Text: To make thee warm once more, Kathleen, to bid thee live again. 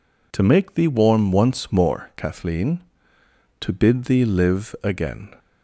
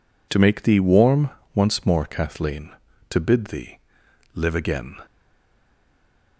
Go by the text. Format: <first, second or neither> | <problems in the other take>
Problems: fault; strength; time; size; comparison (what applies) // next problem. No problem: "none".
first | pauses between "warm" and "once"; slight; at 1.3 s; 0.24 s long // pauses between "thee" and "live"; noticeable; at 3.7 s; 0.56 s long // stays silent after the last word; noticeable; from 5.0 s on; 1.3 s long